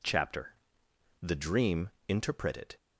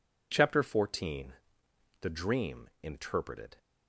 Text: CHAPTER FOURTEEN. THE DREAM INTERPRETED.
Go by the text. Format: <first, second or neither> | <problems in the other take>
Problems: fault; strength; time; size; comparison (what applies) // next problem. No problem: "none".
second | skips "FOURTEEN"; at 0.8 s // pauses between "DREAM" and "INTERPRETED"; slight; at 1.9 s; 0.18 s long